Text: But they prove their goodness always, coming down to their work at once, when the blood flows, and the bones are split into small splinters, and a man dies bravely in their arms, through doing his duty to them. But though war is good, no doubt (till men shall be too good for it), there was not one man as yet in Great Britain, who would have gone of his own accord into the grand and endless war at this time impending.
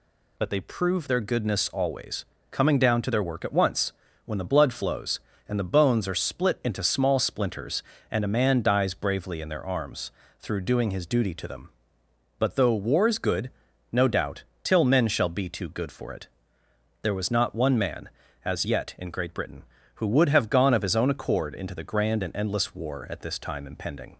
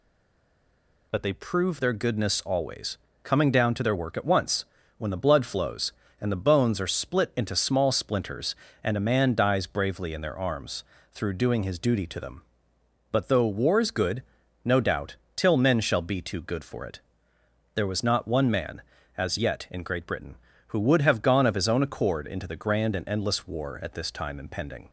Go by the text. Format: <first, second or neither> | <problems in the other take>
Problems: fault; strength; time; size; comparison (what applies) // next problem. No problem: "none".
first | stays silent before the first word; until 1.1 s; 1.1 s long